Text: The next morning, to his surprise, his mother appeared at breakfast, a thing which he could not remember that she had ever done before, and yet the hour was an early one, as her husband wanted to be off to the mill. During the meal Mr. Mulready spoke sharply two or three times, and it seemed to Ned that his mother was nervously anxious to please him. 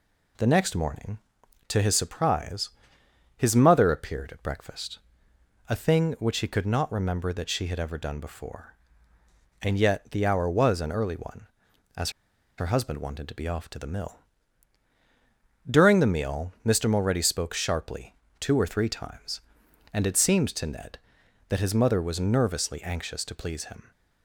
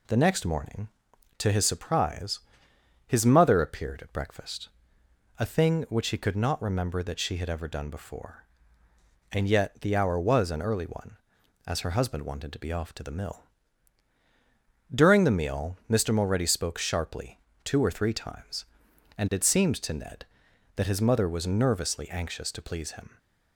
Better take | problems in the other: second | pauses between "as" and "her"; noticeable; at 12.0 s; 0.48 s long // pauses between "sharply" and "two"; slight; at 18.1 s; 0.24 s long; slight in the second

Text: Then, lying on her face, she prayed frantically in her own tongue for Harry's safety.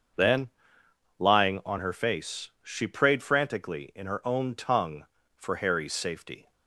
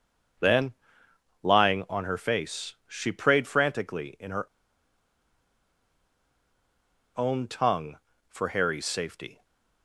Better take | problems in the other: first | starts louder than the rest; until 2.1 s; 6.5 dB; also in the first // pauses between "her" and "own"; strong; at 4.4 s; 2.7 s long // stays silent after the last word; slight; from 9.3 s on; 0.5 s long

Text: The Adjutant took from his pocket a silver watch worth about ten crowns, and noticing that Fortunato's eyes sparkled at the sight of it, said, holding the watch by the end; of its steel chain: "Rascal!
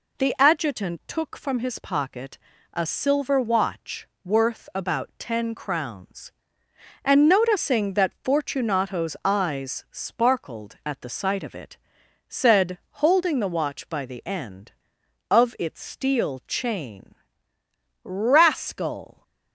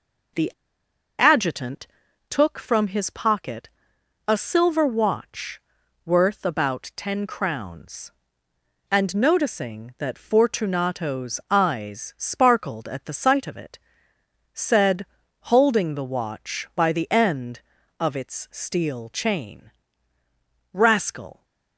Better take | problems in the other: first | pauses between "The" and "Adjutant"; noticeable; at 0.5 s; 0.67 s long // pauses between "Adjutant" and "took"; at 1.8 s; 0.44 s long // pauses between "pocket" and "a"; noticeable; at 3.6 s; 0.58 s long; slight in the first // pauses between "watch" and "worth"; noticeable; at 5.5 s; 0.46 s long; slight in the first

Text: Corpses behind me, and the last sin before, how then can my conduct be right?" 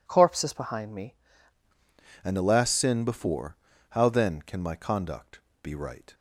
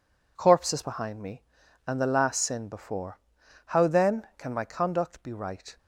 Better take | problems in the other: second | changes voice at "and"; from 2.2 s on; 3.9 s long // pauses between "conduct" and "be"; slight; at 5.3 s; 0.24 s long

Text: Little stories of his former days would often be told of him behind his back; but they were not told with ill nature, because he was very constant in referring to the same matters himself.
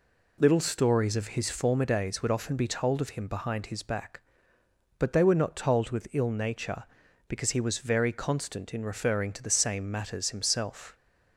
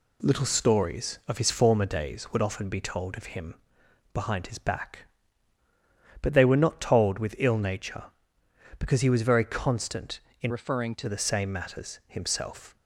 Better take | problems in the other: first | pauses between "him" and "behind"; noticeable; at 3.5 s; 0.58 s long // changes voice from "referring" to "to"; from 10.4 to 11.0 s; 0.6 s long

